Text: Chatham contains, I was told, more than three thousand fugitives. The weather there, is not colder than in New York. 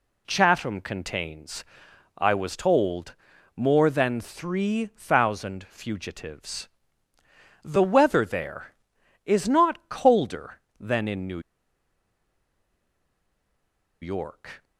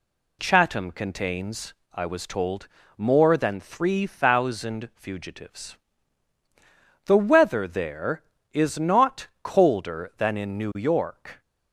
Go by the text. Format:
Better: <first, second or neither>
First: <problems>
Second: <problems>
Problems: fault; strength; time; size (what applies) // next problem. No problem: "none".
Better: second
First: pauses between "New" and "York"; strong; at 11.3 s; 2.6 s long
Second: none